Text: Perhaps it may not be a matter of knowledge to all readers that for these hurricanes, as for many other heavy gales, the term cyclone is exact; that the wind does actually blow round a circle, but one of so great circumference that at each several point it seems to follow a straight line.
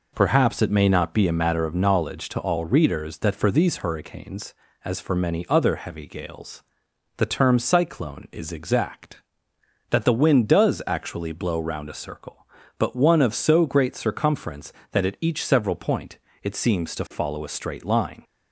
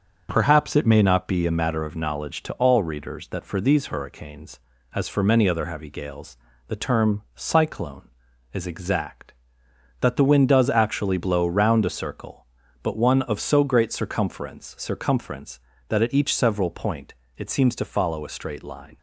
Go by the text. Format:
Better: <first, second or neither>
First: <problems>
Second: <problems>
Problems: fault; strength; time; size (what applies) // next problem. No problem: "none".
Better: first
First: pauses between "point" and "it"; slight; at 16.1 s; 0.26 s long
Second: starts louder than the rest; until 1.3 s; 6.5 dB // says "circumference" twice; at 14.7 s // pauses between "point" and "it"; slight; at 17.1 s; 0.24 s long